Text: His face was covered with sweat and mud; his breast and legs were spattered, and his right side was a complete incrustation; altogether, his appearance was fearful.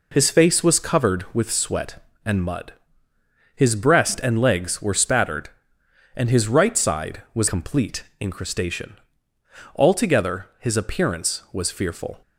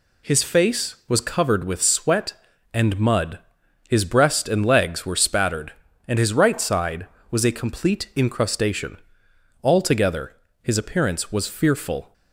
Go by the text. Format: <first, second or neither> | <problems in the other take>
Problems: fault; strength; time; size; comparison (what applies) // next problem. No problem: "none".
second | skips "a"; at 7.4 s